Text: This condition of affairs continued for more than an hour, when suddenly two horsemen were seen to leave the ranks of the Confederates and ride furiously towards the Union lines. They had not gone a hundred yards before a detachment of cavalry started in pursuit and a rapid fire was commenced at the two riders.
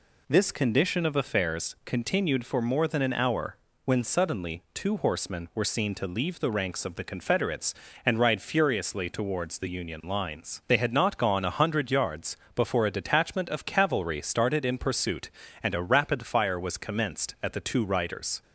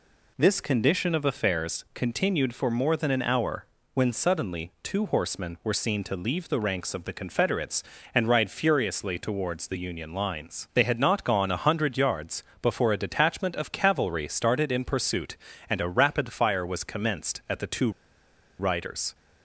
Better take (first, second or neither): first